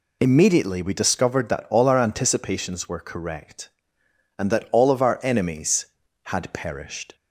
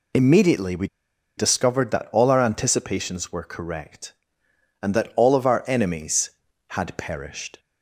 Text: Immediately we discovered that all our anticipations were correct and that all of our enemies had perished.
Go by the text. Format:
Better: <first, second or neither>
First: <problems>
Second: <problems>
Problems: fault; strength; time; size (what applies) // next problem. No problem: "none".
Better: first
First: none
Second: pauses between "we" and "discovered"; noticeable; at 0.8 s; 0.50 s long